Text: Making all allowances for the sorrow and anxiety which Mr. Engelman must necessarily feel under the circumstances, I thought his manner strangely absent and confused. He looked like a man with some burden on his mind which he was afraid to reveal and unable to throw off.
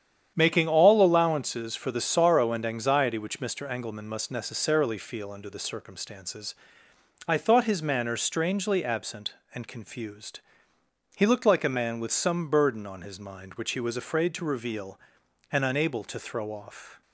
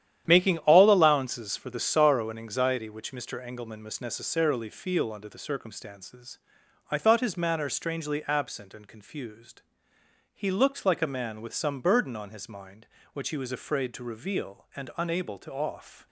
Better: first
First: starts louder than the rest; strong; until 1.3 s; 9 dB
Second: starts louder than the rest; strong; until 1.2 s; 10.5 dB // skips "throw"; at 15.5 s

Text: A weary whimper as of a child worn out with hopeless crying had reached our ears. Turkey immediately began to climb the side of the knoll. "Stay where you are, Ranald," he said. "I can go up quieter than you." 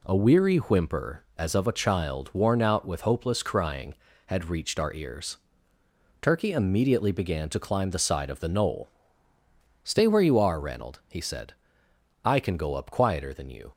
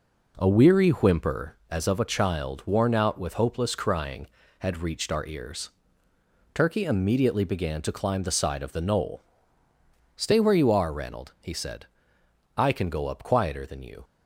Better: first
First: none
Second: starts louder than the rest; noticeable; until 1.5 s; 4.5 dB

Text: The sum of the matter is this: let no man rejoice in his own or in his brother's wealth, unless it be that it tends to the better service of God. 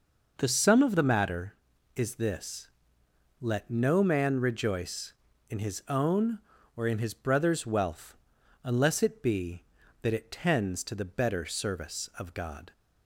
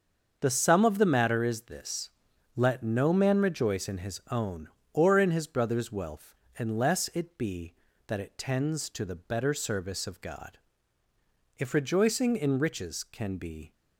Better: first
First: none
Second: starts louder than the rest; until 1.4 s; 6.5 dB // goes on to say "If rejoicing in riches can be"; strong; from 11.5 s on; 2.1 s long

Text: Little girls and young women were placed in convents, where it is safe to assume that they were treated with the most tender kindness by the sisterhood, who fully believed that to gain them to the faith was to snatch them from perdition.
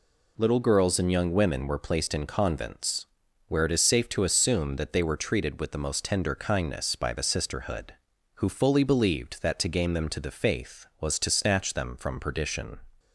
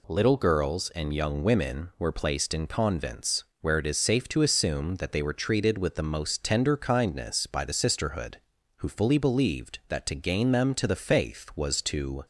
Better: first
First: none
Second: stops before "snatch them from perdition"; at 12.2 s

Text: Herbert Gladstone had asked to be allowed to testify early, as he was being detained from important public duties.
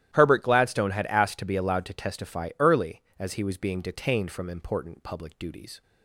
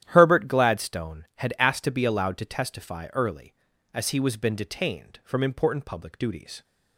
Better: first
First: starts louder than the rest; strong; until 1.1 s; 12.5 dB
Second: starts louder than the rest; strong; until 1.0 s; 11.5 dB // says "been" for "being"; at 4.3 s

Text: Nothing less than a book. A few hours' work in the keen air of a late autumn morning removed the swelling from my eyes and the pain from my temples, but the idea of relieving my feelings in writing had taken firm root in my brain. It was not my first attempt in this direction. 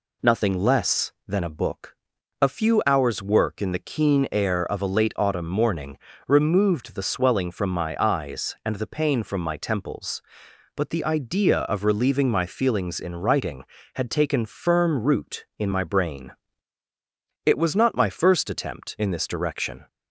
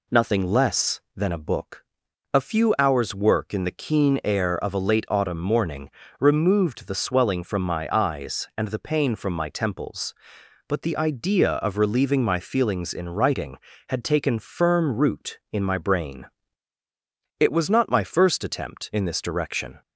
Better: neither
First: pauses between "morning" and "removed"; slight; at 5.9 s; 0.30 s long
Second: pauses between "morning" and "removed"; slight; at 5.8 s; 0.30 s long

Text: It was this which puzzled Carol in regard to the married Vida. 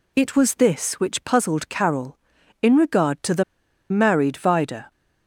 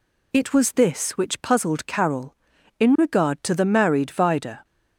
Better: second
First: pauses between "the" and "married"; noticeable; at 3.4 s; 0.48 s long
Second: none

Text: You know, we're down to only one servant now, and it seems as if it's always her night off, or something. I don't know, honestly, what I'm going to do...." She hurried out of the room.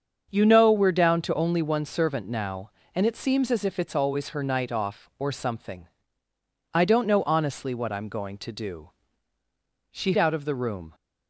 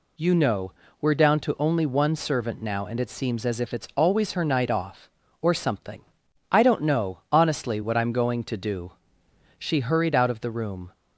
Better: second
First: starts louder than the rest; until 1.3 s; 7 dB // skips "hurried"; at 10.1 s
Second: none

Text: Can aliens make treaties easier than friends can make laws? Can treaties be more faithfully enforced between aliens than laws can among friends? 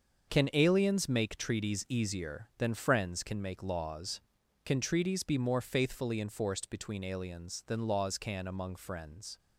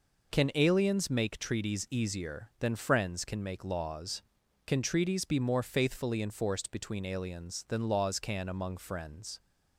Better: second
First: gets quieter; strong; throughout; 8.5 dB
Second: none

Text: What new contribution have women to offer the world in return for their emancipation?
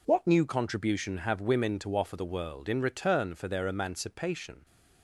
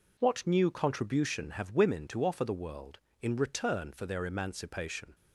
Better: neither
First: none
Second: none

